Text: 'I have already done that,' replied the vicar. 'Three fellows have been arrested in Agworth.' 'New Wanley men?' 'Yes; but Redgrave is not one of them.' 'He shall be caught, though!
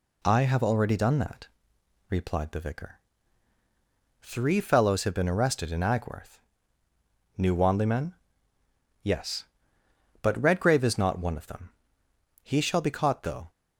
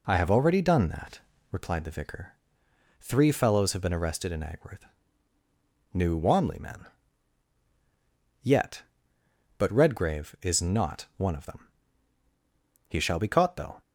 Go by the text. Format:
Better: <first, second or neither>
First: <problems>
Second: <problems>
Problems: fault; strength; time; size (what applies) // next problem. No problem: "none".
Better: first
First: none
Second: says "Yet" for "Yes"; at 8.4 s